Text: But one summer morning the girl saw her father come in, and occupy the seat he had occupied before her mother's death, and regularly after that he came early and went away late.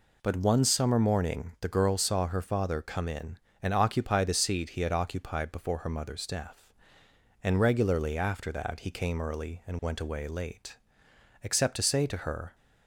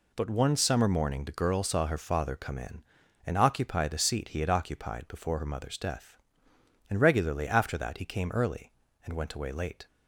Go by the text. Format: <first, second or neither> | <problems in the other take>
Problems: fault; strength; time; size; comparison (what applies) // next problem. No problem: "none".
second | goes on to say "Except to say to her"; noticeable; from 11.4 s on; 1.1 s long